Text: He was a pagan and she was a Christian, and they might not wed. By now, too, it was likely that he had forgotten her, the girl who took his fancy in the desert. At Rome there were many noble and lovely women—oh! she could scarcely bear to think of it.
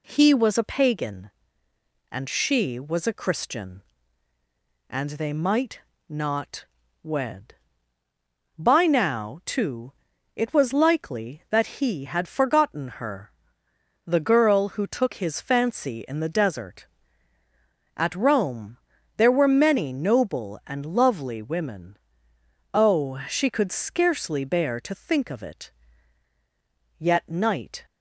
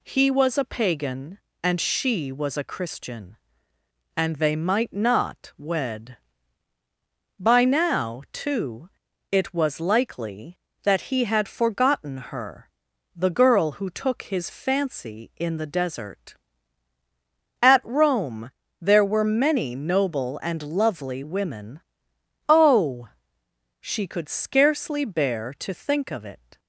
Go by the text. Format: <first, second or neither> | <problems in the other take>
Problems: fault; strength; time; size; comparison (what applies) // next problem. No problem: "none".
second | pauses between "might" and "not"; slight; at 5.8 s; 0.28 s long // pauses between "not" and "wed"; slight; at 6.6 s; 0.36 s long // pauses between "Rome" and "there"; at 18.7 s; 0.40 s long; slight in the second // goes on to say "Yet night"; noticeable; from 26.9 s on; 0.86 s long